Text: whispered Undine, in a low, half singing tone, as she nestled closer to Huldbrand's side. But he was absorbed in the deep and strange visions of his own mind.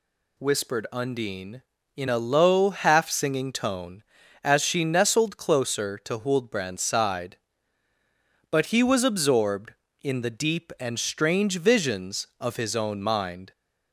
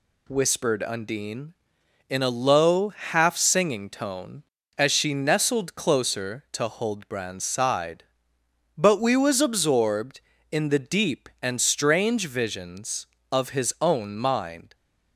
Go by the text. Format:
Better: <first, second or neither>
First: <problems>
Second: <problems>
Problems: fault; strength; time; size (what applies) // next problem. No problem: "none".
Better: first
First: none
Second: says "we" for "he"; at 9.0 s